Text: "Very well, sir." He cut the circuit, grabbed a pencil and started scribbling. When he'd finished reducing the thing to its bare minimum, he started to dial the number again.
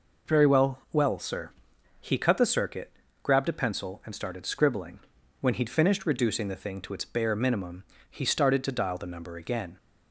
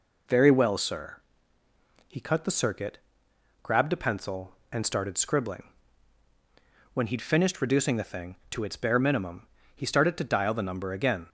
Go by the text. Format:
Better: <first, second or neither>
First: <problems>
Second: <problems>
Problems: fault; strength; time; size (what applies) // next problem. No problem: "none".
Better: second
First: says "well" twice; at 0.9 s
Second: none